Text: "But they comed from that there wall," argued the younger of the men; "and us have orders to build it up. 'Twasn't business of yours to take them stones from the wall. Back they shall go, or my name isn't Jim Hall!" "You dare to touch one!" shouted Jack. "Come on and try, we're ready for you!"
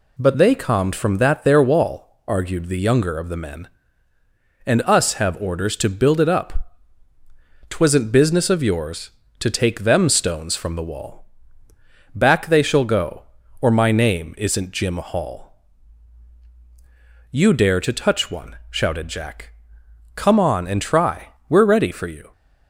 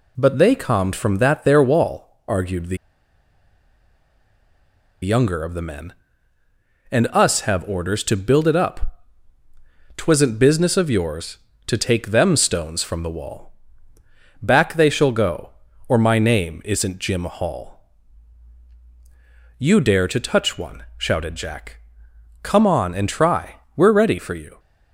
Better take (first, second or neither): first